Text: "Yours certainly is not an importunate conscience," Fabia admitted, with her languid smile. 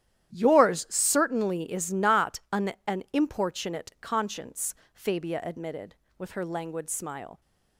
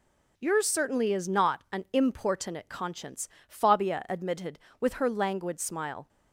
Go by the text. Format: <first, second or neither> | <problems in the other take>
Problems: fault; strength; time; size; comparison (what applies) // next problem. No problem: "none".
second | starts louder than the rest; strong; until 1.3 s; 11.5 dB // says "an" twice; at 2.8 s